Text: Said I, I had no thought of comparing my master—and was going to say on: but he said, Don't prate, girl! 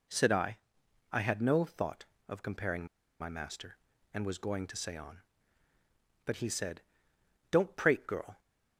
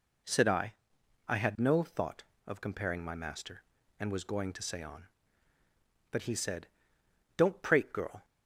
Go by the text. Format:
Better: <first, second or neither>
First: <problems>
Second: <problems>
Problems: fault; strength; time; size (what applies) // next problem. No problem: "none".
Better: second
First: pauses between "comparing" and "my"; slight; at 2.8 s; 0.34 s long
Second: none